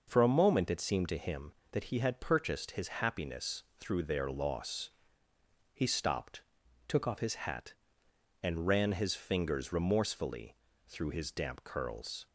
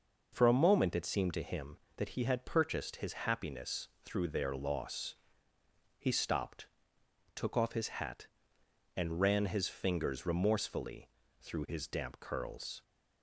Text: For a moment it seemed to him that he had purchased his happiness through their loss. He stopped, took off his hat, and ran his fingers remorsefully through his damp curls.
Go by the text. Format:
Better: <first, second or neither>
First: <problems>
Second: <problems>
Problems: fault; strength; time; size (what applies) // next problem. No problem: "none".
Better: second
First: pauses between "happiness" and "through"; slight; at 3.6 s; 0.16 s long // changes voice from "took" to "off"; from 6.8 to 7.1 s; 0.3 s long // pauses between "remorsefully" and "through"; slight; at 10.5 s; 0.32 s long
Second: pauses between "happiness" and "through"; slight; at 3.8 s; 0.16 s long // pauses between "remorsefully" and "through"; slight; at 11.0 s; 0.32 s long